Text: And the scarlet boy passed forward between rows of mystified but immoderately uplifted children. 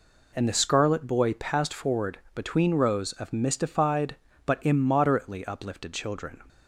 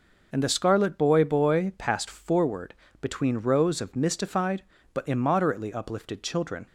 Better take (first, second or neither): first